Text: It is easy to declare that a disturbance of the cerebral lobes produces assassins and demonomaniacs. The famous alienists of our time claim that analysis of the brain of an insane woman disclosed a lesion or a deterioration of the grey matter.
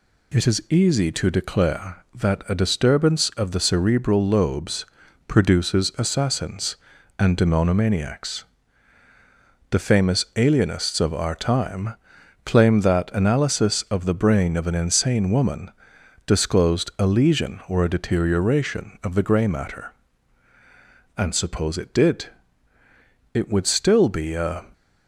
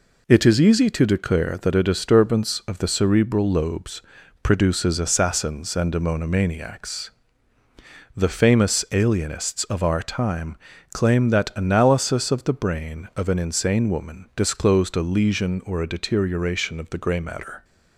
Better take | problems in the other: second | pauses between "lobes" and "produces"; at 4.8 s; 0.40 s long; also in the second // pauses between "time" and "claim"; noticeable; at 11.9 s; 0.48 s long; also in the second // pauses between "woman" and "disclosed"; noticeable; at 15.7 s; 0.54 s long // goes on to say "And suppose it did It would still be a"; strong; from 21.1 s on; 3.5 s long

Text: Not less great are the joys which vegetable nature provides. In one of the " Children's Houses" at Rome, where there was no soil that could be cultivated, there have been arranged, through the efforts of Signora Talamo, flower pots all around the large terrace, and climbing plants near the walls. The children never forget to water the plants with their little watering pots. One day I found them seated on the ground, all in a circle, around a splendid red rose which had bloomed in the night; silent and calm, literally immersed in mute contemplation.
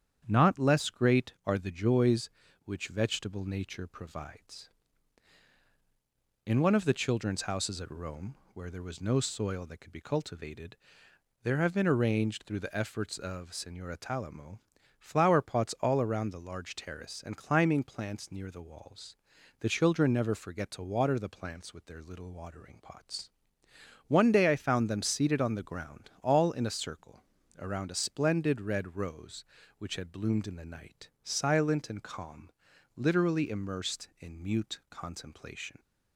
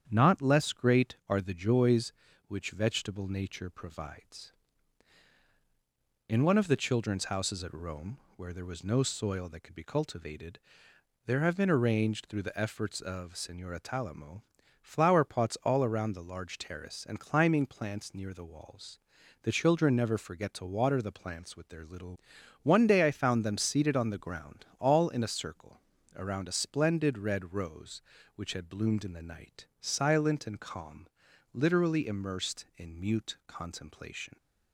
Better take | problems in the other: first | starts louder than the rest; strong; until 1.1 s; 8.5 dB; strong in the first // skips "watering pots"; at 22.3 s

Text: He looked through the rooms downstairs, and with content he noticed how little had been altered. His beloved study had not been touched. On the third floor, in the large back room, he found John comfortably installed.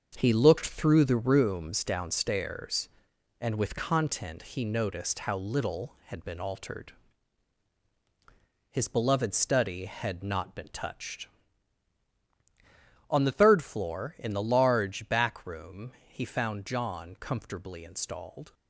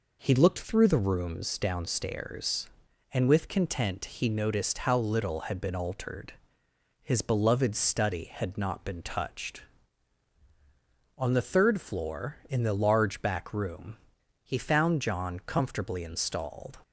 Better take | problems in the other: second | gets quieter; strong; throughout; 7.5 dB

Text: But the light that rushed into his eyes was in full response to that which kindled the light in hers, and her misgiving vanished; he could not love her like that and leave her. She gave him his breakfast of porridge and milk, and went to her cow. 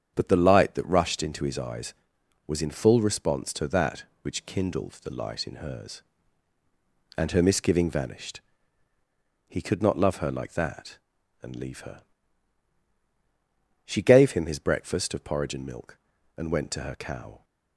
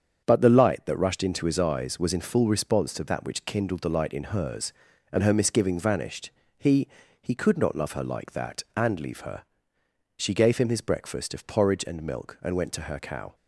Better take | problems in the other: first | starts louder than the rest; strong; until 1.2 s; 7.5 dB; strong in the first // says "he" twice; at 7.2 s

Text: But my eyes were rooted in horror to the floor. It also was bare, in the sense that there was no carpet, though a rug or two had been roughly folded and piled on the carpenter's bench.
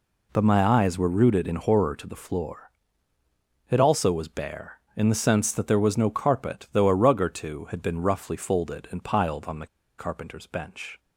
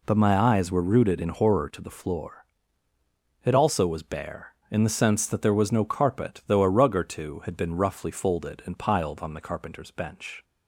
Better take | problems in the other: second | pauses between "the" and "carpenter's"; slight; at 9.6 s; 0.32 s long

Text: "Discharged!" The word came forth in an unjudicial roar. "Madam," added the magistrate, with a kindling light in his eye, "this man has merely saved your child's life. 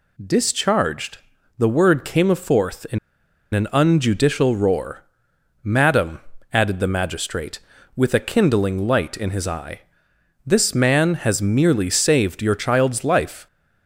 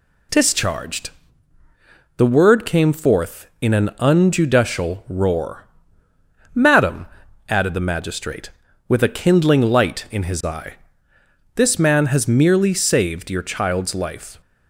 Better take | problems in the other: second | pauses between "in" and "an"; noticeable; at 2.9 s; 0.56 s long

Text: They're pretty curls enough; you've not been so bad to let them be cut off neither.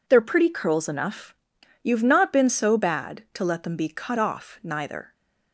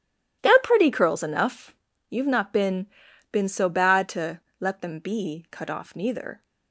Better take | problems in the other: first | says "been" twice; at 3.3 s // pauses between "to" and "let"; slight; at 4.4 s; 0.20 s long

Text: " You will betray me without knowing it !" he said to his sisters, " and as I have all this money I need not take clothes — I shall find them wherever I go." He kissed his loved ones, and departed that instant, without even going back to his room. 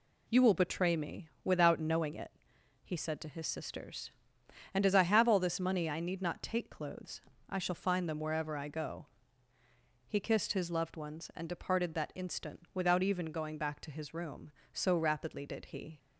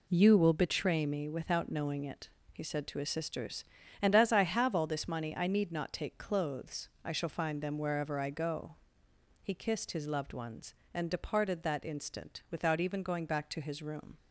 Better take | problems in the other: second | goes on to say "So rapidly did he"; noticeable; from 14.7 s on; 1.2 s long

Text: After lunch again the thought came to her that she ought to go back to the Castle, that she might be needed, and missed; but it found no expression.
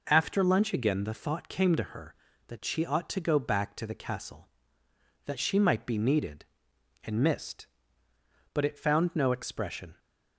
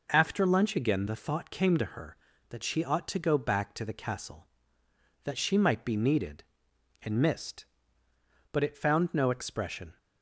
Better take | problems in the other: neither | none

